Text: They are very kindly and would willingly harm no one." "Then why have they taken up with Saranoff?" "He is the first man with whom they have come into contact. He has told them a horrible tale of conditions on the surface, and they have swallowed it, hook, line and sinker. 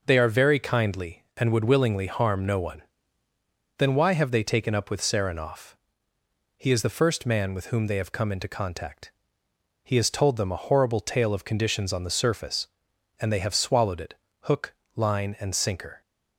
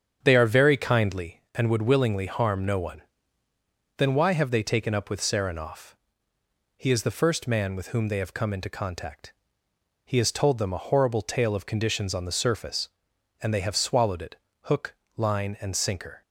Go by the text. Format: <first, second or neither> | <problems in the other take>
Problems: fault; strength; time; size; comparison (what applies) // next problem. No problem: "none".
first | starts louder than the rest; strong; until 1.4 s; 8 dB